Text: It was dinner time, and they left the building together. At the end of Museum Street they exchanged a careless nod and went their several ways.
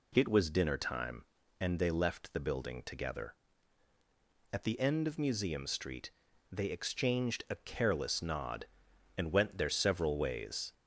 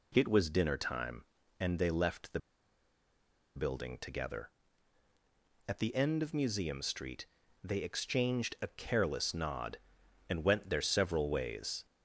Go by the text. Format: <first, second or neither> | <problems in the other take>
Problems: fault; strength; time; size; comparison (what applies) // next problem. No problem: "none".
first | pauses between "the" and "building"; at 2.3 s; 1.1 s long // pauses between "Street" and "they"; slight; at 7.2 s; 0.36 s long; also in the first